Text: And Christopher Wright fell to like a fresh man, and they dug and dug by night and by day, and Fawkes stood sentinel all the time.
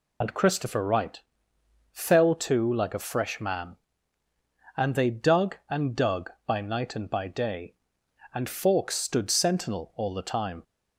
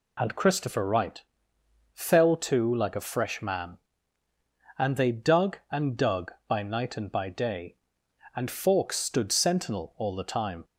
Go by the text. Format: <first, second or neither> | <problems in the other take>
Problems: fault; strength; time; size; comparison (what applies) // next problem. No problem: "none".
second | loses the start of "And"; at 0.2 s; 45 ms // pauses between "Wright" and "fell"; noticeable; at 1.2 s; 0.72 s long; noticeable in the second